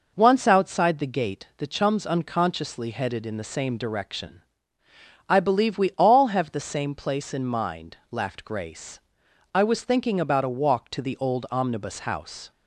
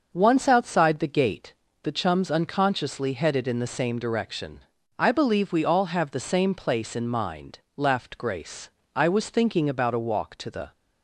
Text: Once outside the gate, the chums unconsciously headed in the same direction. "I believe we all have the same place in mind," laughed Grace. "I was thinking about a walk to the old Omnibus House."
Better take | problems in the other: first | starts louder than the rest; noticeable; until 1.1 s; 6 dB // stops before "old Omnibus House"; at 10.7 s

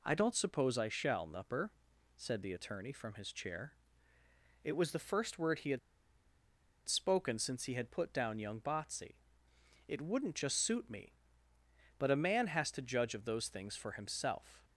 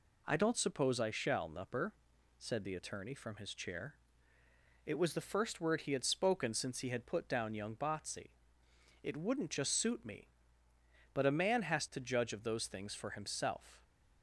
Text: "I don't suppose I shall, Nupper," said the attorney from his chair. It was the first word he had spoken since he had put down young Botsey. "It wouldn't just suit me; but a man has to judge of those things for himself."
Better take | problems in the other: second | pauses between "had" and "spoken"; at 5.7 s; 1.0 s long

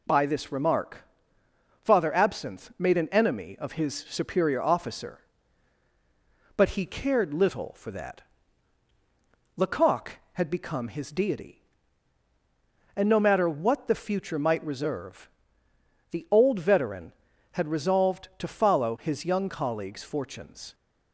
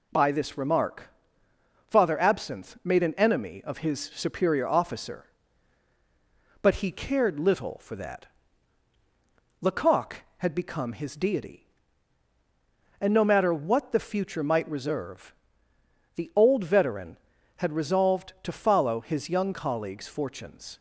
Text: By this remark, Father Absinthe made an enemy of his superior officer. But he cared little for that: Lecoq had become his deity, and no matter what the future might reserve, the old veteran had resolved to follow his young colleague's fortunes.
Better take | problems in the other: neither | none

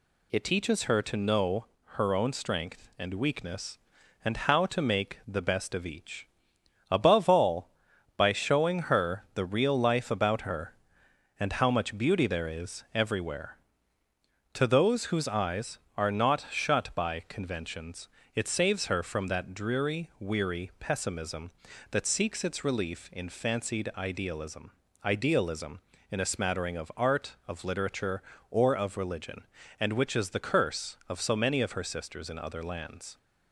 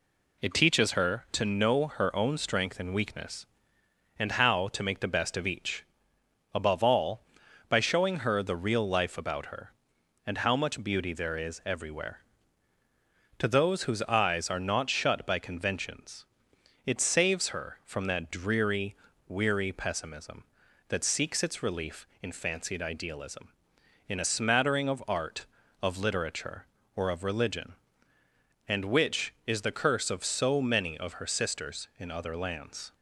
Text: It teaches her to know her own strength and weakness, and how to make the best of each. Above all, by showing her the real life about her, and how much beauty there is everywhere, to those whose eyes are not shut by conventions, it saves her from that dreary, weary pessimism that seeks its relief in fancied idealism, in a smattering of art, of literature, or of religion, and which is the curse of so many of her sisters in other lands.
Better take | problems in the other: second | pauses between "know" and "her"; slight; at 1.6 s; 0.30 s long // says "idealism" twice; at 25.0 s

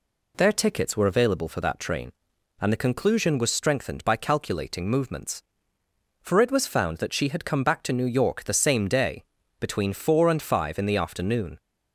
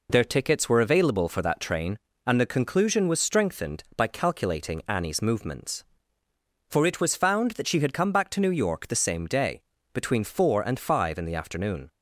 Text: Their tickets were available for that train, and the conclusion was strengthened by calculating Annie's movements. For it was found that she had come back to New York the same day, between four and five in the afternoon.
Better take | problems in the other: second | skips "Annie's"; at 4.8 s

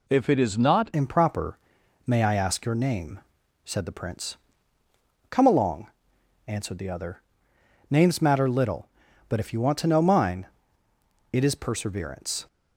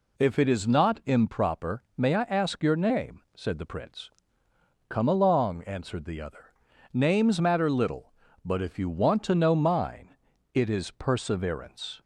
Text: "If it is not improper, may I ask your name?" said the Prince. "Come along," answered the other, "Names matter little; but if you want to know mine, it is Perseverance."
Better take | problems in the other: second | changes voice at "improper"; from 0.9 s on; 11.5 s long

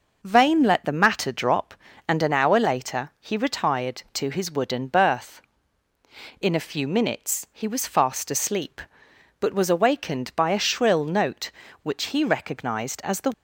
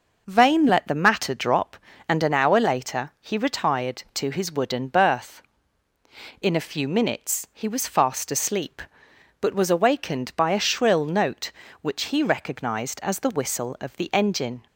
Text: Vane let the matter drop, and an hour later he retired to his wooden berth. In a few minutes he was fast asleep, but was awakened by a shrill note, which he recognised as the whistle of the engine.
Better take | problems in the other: second | stops before "whistle of the engine"; at 13.3 s

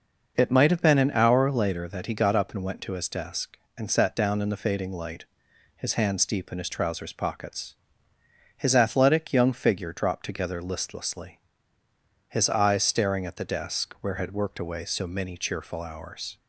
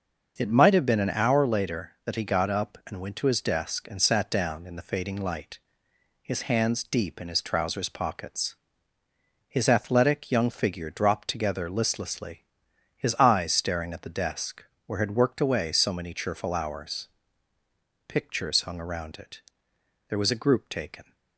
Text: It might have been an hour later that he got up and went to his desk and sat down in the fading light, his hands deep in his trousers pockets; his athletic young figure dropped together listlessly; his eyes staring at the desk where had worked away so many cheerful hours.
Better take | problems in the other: first | starts louder than the rest; noticeable; until 1.3 s; 6 dB // pauses between "desk" and "where"; slight; at 14.6 s; 0.22 s long // goes on to say "Pictures hung around it there was a group taken"; strong; from 18.0 s on; 3.0 s long

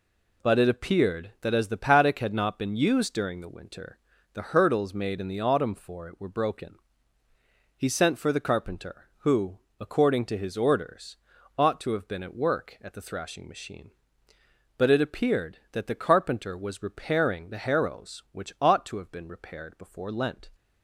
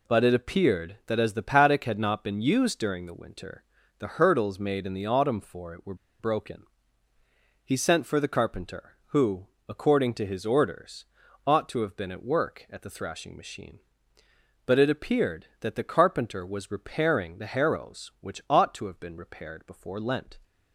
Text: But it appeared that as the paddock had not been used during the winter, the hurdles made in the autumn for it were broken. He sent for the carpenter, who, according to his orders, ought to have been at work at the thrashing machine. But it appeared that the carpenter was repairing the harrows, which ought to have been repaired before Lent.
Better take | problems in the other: first | pauses between "were" and "broken"; slight; at 5.9 s; 0.24 s long

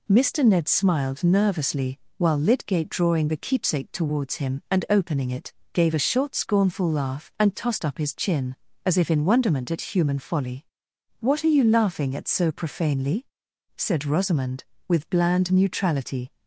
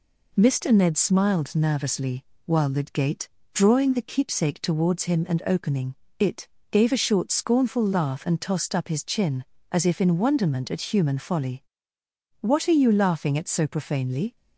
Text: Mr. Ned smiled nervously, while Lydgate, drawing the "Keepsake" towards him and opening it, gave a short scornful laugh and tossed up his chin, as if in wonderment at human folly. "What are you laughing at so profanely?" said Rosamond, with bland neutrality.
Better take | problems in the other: first | pauses between "opening" and "it"; slight; at 5.9 s; 0.24 s long // stops before "said Rosamond with bland neutrality"; at 14.3 s

